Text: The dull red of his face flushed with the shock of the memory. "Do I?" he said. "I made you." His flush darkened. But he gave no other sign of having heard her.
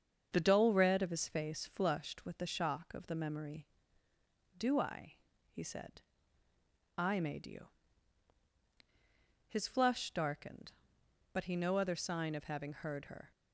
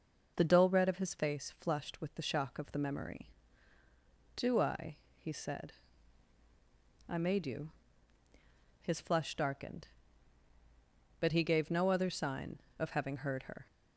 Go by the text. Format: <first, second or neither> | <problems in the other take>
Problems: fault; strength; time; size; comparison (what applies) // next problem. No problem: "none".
second | starts louder than the rest; strong; until 1.3 s; 7 dB // skips "gave"; at 11.5 s